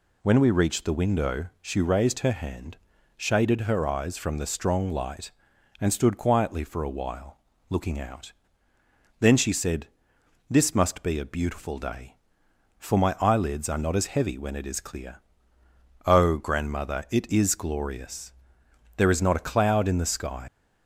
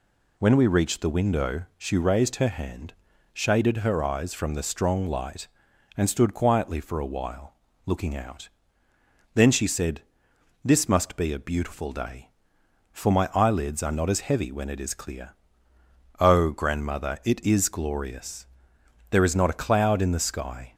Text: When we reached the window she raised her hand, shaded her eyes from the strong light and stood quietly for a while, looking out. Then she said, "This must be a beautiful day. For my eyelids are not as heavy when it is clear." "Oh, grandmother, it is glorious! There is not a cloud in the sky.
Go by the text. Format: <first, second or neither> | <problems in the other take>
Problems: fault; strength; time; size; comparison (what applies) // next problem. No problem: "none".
second | leaves "sky" unfinished; at 20.4 s; 125 ms